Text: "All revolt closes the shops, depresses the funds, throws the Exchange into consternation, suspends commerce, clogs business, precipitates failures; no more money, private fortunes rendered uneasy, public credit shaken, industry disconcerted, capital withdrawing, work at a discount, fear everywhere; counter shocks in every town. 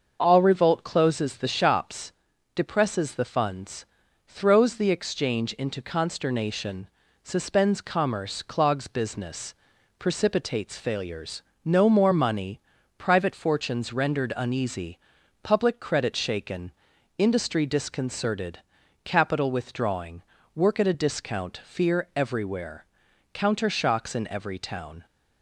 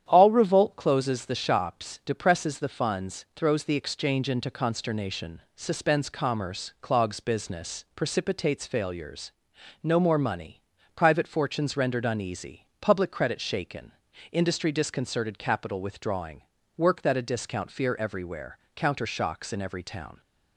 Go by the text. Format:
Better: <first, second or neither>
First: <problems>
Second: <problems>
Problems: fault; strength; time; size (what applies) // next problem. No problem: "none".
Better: first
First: starts louder than the rest; until 1.2 s; 6.5 dB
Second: starts louder than the rest; strong; until 1.0 s; 9.5 dB // says "that" for "at"; at 17.0 s